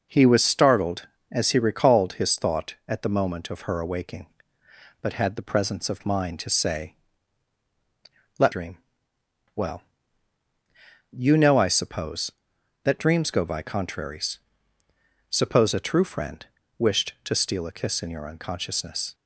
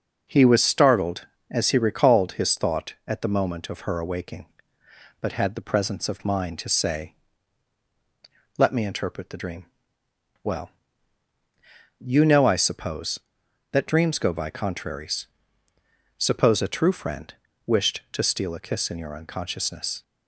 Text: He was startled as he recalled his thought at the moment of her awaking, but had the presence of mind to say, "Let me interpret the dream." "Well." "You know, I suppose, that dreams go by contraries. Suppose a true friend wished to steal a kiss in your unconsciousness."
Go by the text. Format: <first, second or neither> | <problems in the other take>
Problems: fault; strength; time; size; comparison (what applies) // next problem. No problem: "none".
second | skips "me interpret the"; at 8.5 s // pauses between "friend" and "wished"; slight; at 16.4 s; 0.32 s long; slight in the second